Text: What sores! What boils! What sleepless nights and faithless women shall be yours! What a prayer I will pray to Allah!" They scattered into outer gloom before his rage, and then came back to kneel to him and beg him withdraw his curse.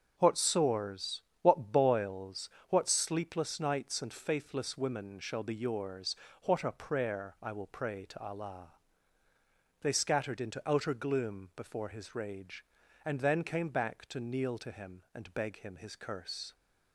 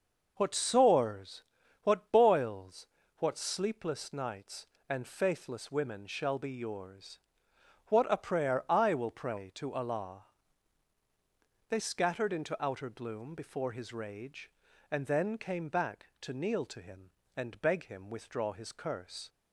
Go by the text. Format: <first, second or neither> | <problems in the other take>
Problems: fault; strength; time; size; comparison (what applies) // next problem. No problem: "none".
second | starts louder than the rest; until 1.1 s; 6.5 dB // skips "withdraw"; at 15.7 s